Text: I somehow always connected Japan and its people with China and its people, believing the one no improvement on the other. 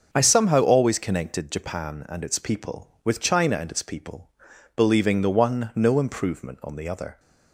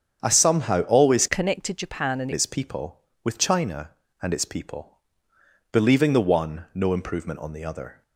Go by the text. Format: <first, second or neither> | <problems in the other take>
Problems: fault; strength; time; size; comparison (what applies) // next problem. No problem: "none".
first | starts louder than the rest; strong; until 1.2 s; 7.5 dB; also in the first // changes voice from "connected" to "and"; from 1.2 to 2.2 s; 1.0 s long